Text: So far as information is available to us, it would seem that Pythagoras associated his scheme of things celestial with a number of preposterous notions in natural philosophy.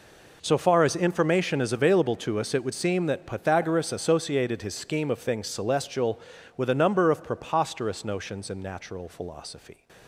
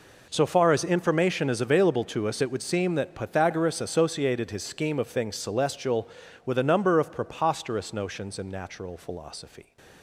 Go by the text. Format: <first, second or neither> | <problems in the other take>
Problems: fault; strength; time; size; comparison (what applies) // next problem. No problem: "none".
neither | none